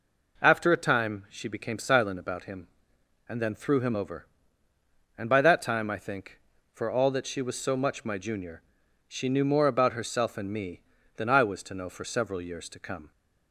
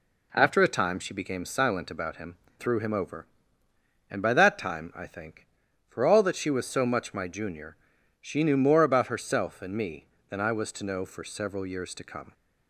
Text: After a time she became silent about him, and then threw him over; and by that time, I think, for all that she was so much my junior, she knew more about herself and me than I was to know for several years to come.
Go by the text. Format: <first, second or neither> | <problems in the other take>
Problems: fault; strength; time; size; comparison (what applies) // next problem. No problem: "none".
first | skips "and then"; at 2.4 s